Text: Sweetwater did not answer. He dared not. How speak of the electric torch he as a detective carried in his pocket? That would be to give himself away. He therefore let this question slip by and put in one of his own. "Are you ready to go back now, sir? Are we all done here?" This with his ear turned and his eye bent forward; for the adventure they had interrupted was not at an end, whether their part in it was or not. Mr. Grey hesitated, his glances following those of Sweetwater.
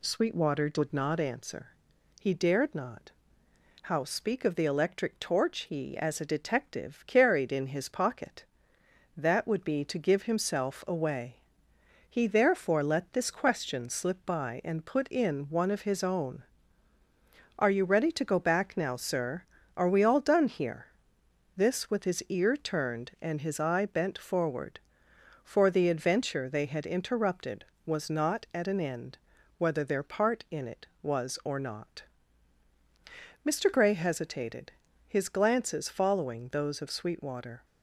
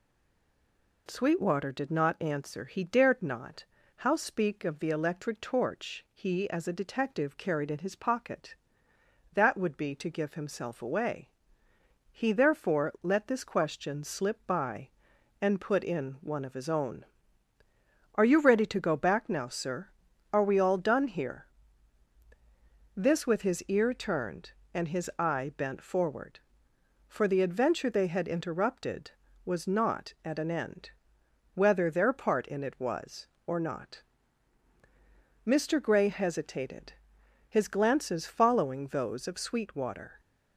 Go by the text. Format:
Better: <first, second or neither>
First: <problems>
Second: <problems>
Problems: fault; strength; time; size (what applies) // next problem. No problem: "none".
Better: first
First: none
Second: stays silent before the first word; until 1.0 s; 1.0 s long